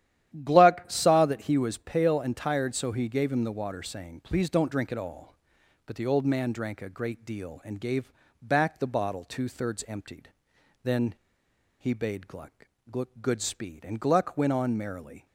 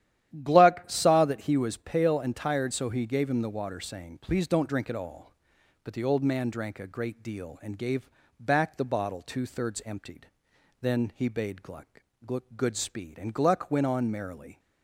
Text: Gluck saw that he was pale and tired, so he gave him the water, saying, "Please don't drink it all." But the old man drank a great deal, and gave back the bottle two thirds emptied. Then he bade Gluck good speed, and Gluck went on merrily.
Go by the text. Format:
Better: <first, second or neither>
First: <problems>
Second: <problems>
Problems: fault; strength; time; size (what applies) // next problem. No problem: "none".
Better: second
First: starts louder than the rest; strong; until 1.4 s; 11.5 dB // pauses between "gave" and "back"; slight; at 8.1 s; 0.30 s long // pauses between "Then" and "he"; noticeable; at 11.1 s; 0.68 s long // pauses between "Gluck" and "good"; noticeable; at 12.6 s; 0.52 s long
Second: starts louder than the rest; strong; until 1.4 s; 11.5 dB // pauses between "gave" and "back"; slight; at 8.0 s; 0.30 s long // pauses between "Gluck" and "good"; noticeable; at 12.0 s; 0.52 s long